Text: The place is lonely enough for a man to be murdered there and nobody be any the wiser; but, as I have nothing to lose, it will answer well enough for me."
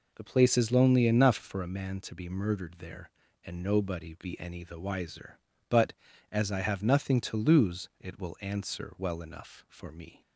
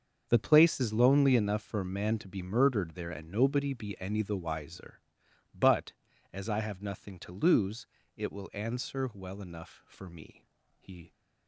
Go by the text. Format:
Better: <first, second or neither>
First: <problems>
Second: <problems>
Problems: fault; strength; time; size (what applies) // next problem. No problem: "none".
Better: first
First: none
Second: starts louder than the rest; until 1.3 s; 6.5 dB // goes on to say "He"; slight; from 10.7 s on; 0.34 s long